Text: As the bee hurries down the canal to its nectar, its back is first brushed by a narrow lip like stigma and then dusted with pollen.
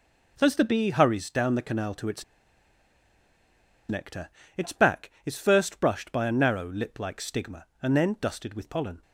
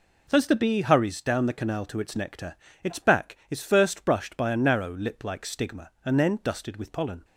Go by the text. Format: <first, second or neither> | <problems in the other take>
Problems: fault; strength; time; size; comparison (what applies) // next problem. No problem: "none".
second | pauses between "its" and "nectar"; strong; at 2.2 s; 1.6 s long